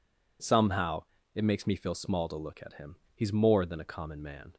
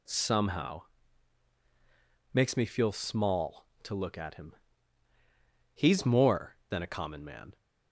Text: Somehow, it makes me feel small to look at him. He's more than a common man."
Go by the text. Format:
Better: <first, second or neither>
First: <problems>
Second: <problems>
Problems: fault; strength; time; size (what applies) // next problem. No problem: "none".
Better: first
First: none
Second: skips "it"; at 1.5 s